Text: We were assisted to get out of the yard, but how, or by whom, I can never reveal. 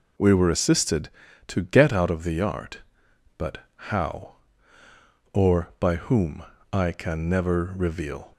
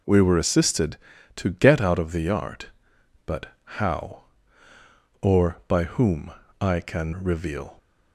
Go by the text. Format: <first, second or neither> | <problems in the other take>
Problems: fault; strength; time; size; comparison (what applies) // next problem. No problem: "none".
first | pauses between "but" and "how"; slight; at 3.4 s; 0.18 s long; slight in the first // skips "never"; at 7.1 s